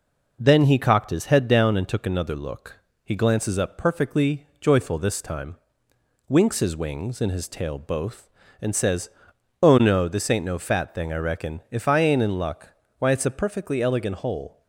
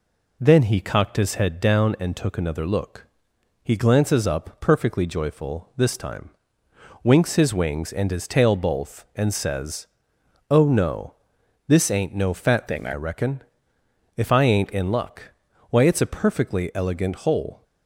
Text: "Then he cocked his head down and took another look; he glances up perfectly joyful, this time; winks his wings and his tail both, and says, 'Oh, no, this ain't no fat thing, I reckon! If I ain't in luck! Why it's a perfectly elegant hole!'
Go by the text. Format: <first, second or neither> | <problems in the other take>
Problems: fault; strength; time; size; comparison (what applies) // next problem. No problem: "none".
first | changes voice from "thing" to "I"; from 12.6 to 12.9 s; 0.3 s long